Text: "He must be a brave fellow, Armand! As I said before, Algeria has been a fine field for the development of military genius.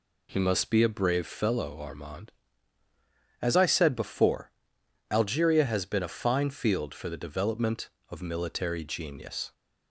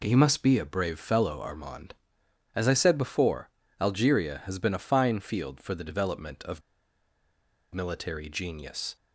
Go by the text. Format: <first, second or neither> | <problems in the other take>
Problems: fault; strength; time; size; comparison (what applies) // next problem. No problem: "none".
first | pauses between "of" and "military"; at 6.6 s; 1.1 s long